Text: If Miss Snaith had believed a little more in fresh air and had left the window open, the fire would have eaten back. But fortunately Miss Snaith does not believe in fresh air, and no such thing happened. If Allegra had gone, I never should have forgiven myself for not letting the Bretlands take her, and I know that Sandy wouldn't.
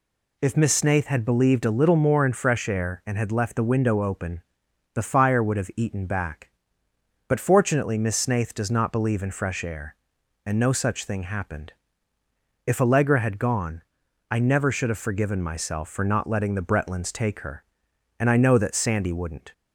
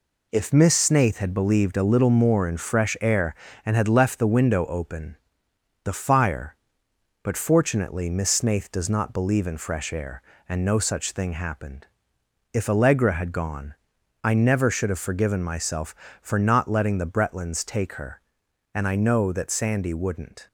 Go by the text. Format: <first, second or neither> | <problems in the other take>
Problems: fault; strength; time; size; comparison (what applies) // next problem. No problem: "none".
first | skips "would have eaten back"; at 6.8 s